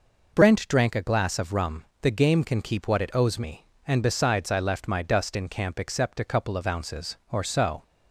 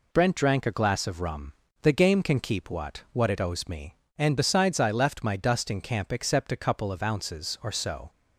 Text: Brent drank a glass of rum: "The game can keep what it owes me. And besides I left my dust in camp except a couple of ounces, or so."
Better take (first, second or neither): first